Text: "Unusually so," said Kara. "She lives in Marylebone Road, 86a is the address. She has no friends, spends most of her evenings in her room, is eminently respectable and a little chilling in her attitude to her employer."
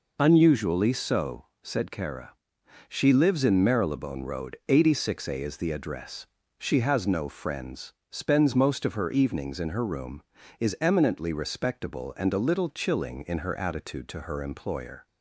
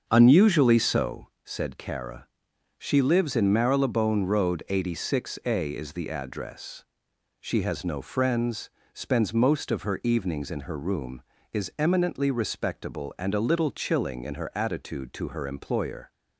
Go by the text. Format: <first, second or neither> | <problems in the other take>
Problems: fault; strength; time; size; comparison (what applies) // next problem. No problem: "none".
first | starts louder than the rest; until 1.1 s; 7 dB